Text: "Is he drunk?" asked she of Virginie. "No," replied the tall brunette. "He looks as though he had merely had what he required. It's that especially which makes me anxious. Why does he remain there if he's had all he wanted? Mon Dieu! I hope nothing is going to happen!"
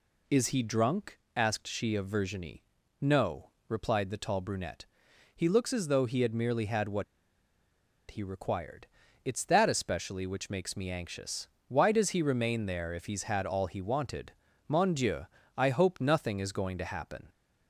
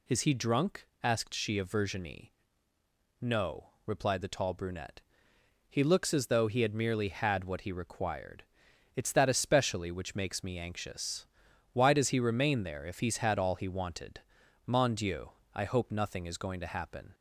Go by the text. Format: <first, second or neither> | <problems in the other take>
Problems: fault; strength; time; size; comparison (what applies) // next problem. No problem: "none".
second | pauses between "what" and "he"; at 7.0 s; 1.0 s long